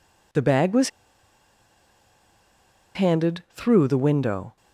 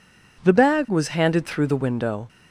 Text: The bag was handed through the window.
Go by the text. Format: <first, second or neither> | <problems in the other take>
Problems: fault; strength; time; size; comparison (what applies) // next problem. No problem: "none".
second | pauses between "was" and "handed"; strong; at 0.8 s; 2.0 s long